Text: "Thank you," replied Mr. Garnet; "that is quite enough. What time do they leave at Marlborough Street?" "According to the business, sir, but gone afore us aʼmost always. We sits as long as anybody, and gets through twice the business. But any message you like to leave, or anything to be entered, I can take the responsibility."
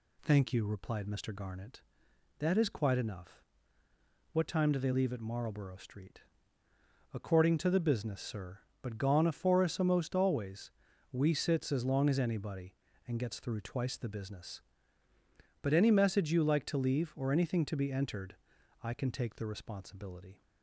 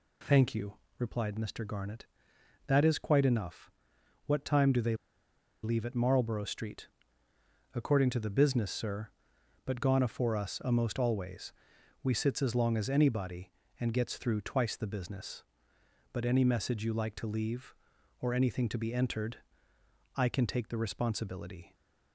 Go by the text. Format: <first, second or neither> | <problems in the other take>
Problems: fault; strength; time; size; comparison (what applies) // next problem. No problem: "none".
first | pauses between "they" and "leave"; noticeable; at 4.9 s; 0.69 s long